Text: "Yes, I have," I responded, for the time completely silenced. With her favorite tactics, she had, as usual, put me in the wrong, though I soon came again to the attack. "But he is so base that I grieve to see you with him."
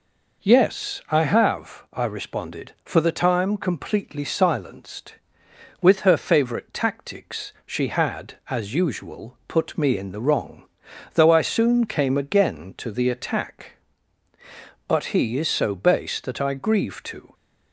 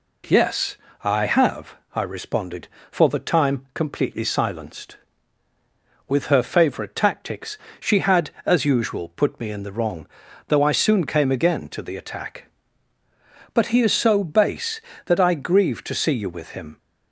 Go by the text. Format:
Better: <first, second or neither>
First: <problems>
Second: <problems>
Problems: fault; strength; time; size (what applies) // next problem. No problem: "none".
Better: second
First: stops before "see you with him"; at 17.3 s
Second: none